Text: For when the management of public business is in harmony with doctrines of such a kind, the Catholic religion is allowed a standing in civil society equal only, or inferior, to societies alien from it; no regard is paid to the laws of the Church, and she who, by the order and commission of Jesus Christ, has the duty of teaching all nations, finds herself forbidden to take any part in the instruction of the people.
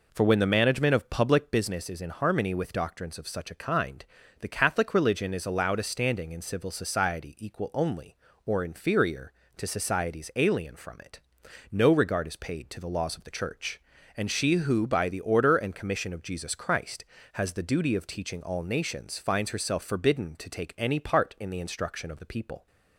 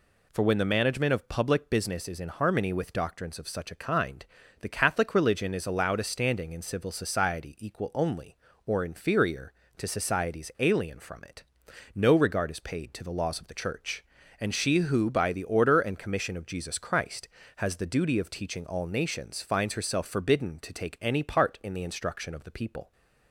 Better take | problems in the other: second | starts louder than the rest; noticeable; until 1.6 s; 4.5 dB

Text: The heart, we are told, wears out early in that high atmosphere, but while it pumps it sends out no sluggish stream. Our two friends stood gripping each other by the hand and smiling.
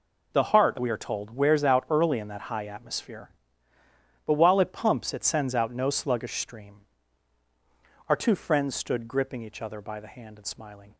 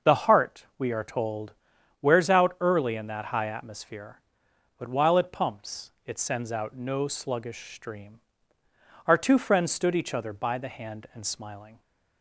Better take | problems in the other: first | pauses between "pumps" and "it"; slight; at 5.9 s; 0.16 s long // skips "gripping"; at 9.9 s

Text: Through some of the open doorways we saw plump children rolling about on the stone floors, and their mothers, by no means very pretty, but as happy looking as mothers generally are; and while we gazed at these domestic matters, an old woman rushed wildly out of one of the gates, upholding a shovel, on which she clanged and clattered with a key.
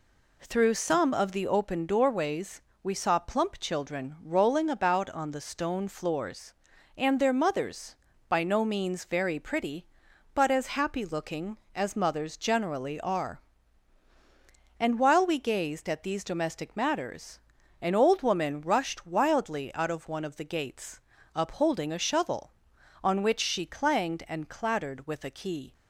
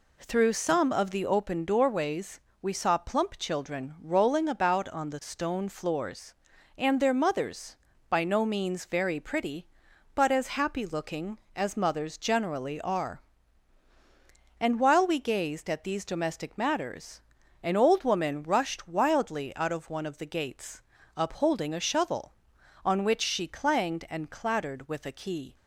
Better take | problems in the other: neither | pauses between "doorways" and "we"; slight; the same in both

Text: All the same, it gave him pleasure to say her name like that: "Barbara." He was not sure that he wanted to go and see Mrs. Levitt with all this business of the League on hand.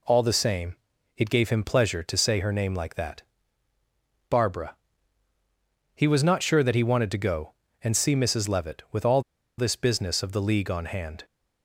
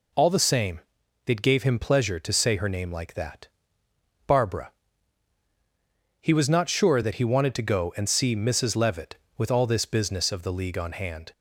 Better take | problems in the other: second | pauses between "all" and "this"; at 9.2 s; 0.37 s long

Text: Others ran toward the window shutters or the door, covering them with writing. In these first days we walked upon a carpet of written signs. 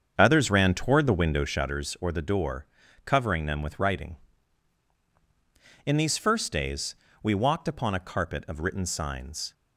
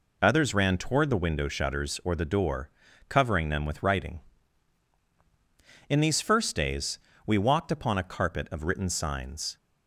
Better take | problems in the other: second | starts louder than the rest; strong; until 1.7 s; 7 dB // pauses between "days" and "we"; slight; at 6.9 s; 0.28 s long; slight in the second

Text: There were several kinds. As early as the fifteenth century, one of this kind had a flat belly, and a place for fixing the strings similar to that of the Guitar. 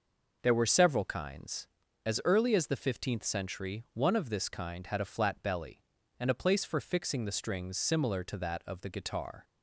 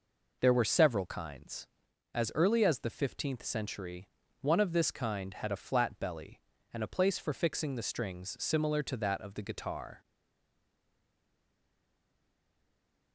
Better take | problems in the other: first | stays silent after the last word; strong; from 10.0 s on; 3.1 s long

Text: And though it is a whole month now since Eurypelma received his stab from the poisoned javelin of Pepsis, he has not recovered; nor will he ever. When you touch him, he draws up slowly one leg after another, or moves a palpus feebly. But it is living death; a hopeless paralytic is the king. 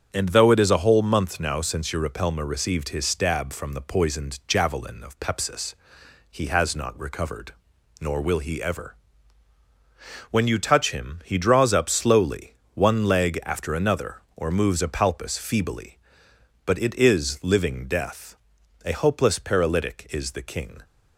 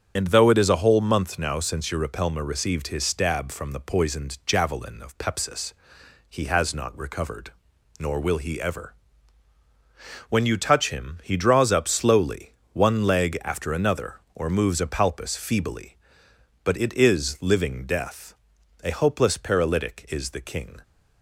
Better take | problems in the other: first | loses the start of "And"; at 0.1 s; 30 ms // starts louder than the rest; strong; until 1.1 s; 8 dB; strong in the first // pauses between "slowly" and "one"; slight; at 12.5 s; 0.20 s long; slight in the first

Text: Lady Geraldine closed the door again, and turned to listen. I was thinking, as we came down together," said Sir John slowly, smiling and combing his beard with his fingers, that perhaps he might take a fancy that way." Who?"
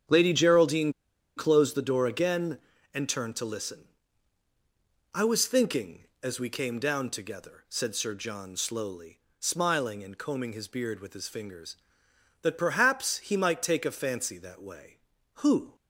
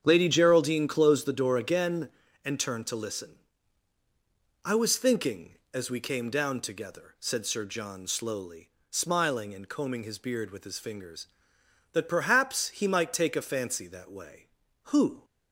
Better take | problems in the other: second | starts louder than the rest; strong; until 1.5 s; 8 dB; strong in the second // pauses between "Geraldine" and "closed"; at 0.9 s; 0.44 s long

